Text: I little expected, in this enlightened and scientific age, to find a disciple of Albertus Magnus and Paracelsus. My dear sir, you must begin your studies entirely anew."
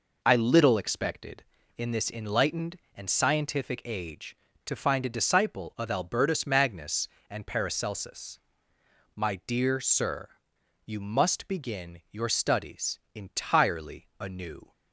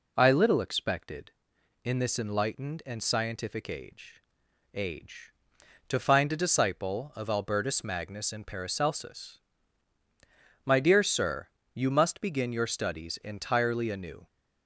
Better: first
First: none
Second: says "age" twice; at 4.7 s

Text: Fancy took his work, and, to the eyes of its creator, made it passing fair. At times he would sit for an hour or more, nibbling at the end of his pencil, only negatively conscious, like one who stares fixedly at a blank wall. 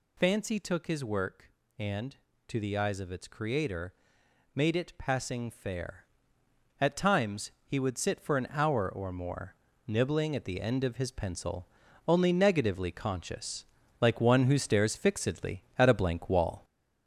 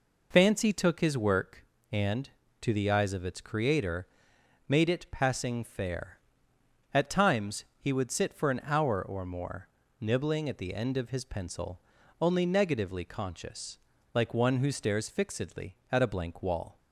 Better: second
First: gets louder; noticeable; throughout; 5 dB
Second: none

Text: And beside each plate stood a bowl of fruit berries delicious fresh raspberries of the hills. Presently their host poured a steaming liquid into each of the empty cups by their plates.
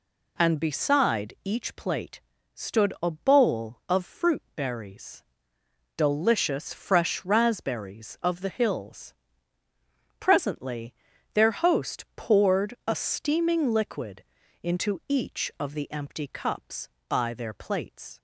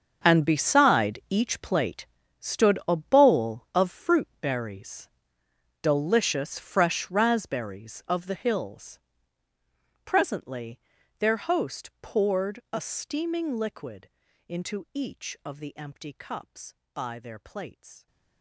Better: first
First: pauses between "plate" and "stood"; slight; at 2.2 s; 0.32 s long // pauses between "berries" and "delicious"; noticeable; at 5.2 s; 0.72 s long // pauses between "Presently" and "their"; at 10.9 s; 0.40 s long // pauses between "liquid" and "into"; at 14.2 s; 0.38 s long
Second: gets quieter; strong; throughout; 16.5 dB // pauses between "plate" and "stood"; slight; at 2.0 s; 0.32 s long // pauses between "berries" and "delicious"; noticeable; at 5.0 s; 0.72 s long // pauses between "Presently" and "their"; at 10.7 s; 0.40 s long // pauses between "liquid" and "into"; at 14.0 s; 0.38 s long

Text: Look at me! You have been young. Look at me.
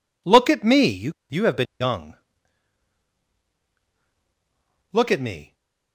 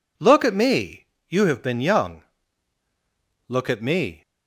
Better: second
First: says "You" twice; at 1.2 s // stays silent after the last word; slight; from 5.4 s on; 0.5 s long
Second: none

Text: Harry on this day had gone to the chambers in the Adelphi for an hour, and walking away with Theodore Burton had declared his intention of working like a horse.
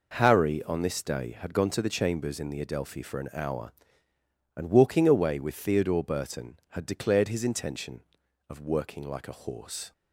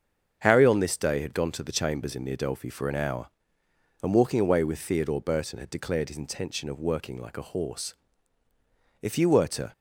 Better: first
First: none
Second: starts louder than the rest; until 1.4 s; 6.5 dB // goes on to say "If you were to"; noticeable; from 9.0 s on; 0.70 s long

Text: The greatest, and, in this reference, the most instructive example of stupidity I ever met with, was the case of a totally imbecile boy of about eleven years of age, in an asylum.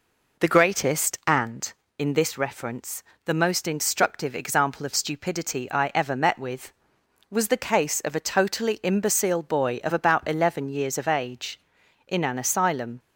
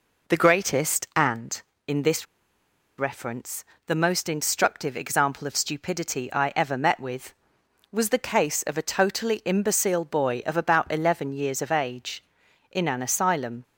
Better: first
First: none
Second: pauses between "this" and "reference"; noticeable; at 2.2 s; 0.72 s long

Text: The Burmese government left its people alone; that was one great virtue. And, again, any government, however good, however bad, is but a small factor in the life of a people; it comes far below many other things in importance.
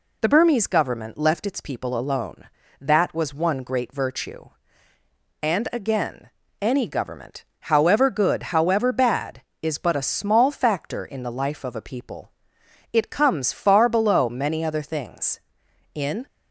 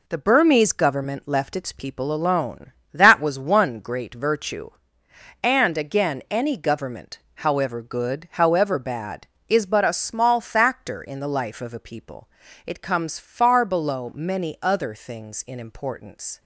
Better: second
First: stops before "importance"; at 16.2 s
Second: none

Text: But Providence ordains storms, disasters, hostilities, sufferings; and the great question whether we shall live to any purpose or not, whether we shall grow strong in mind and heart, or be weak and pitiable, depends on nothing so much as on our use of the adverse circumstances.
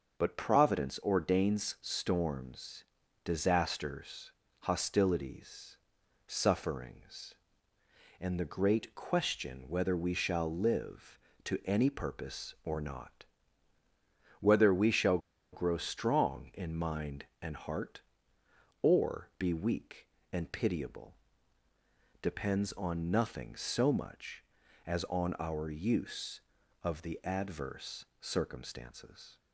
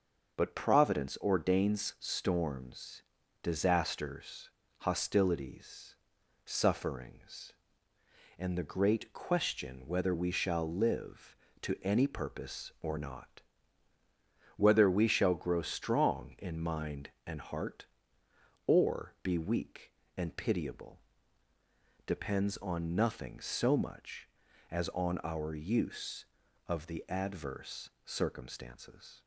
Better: second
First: starts louder than the rest; until 1.2 s; 6 dB // pauses between "shall" and "grow"; slight; at 15.1 s; 0.34 s long // pauses between "adverse" and "circumstances"; slight; at 28.0 s; 0.16 s long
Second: starts louder than the rest; until 1.4 s; 6 dB // pauses between "adverse" and "circumstances"; slight; at 27.9 s; 0.16 s long

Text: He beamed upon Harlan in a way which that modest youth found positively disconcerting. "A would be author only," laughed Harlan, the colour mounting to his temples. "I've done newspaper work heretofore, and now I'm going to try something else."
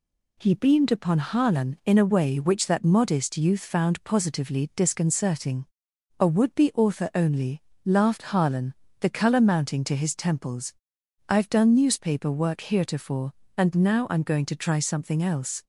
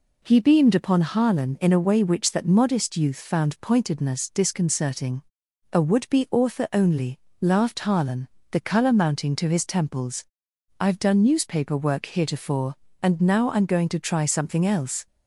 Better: first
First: none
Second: says "pointedness" for "positively"; at 3.6 s

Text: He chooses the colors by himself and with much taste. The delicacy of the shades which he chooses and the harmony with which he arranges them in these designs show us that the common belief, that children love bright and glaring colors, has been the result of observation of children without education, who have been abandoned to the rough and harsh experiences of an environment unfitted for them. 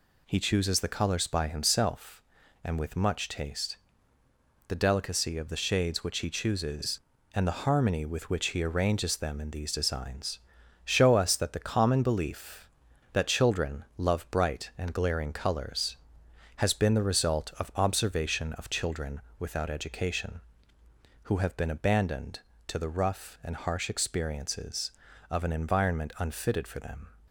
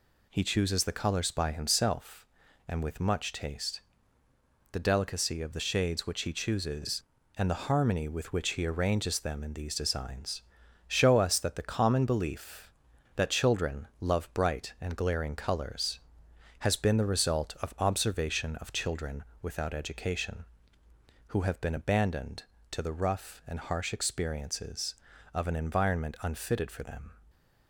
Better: neither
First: pauses between "designs" and "show"; at 10.3 s; 0.44 s long // pauses between "children" and "without"; slight; at 19.1 s; 0.18 s long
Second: pauses between "designs" and "show"; at 10.4 s; 0.44 s long // pauses between "children" and "without"; slight; at 19.2 s; 0.18 s long

